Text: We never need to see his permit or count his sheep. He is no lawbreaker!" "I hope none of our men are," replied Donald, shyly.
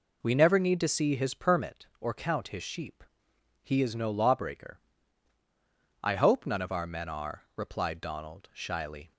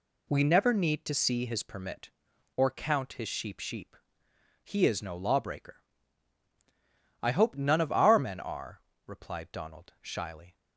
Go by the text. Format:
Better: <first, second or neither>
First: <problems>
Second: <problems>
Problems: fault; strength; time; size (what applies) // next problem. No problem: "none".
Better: first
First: none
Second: says "sheep" twice; at 3.6 s